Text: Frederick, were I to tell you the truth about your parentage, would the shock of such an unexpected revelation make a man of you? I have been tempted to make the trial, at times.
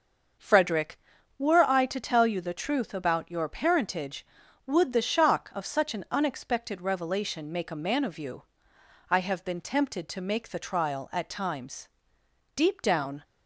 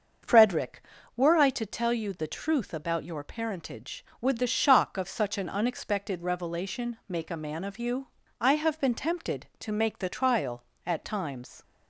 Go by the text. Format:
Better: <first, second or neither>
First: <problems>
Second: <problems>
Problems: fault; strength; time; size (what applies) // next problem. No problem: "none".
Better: second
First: starts louder than the rest; until 1.7 s; 6.5 dB // goes on to say "Deep down"; noticeable; from 12.5 s on; 0.70 s long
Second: starts louder than the rest; until 1.6 s; 6.5 dB